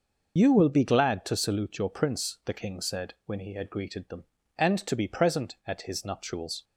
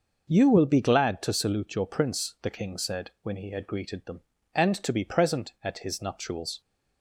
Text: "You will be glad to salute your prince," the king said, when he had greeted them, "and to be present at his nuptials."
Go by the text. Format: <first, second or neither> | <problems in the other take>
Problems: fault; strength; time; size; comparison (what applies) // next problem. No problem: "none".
second | loses the start of "You"; at 0.3 s; 40 ms